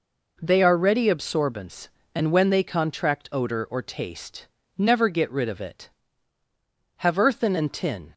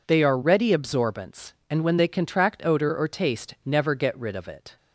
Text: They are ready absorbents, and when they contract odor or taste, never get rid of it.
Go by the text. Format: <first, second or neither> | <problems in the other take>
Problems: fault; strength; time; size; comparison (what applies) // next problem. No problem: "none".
second | goes on to say "Have earthen and tin"; noticeable; from 6.9 s on; 1.1 s long